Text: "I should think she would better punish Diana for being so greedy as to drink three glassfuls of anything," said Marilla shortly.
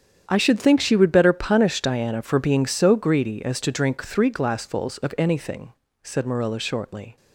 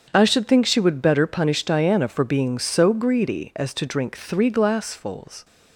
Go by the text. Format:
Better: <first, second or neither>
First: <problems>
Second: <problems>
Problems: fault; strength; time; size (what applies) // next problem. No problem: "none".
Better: first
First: starts louder than the rest; strong; until 1.2 s; 8.5 dB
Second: starts louder than the rest; strong; until 1.1 s; 7.5 dB // stops before "of anything said Marilla shortly"; at 5.4 s